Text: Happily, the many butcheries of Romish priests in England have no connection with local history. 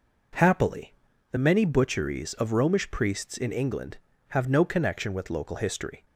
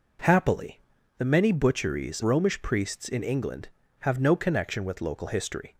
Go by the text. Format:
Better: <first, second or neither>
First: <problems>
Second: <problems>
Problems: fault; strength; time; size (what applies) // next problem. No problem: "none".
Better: first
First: none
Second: skips "of"; at 2.2 s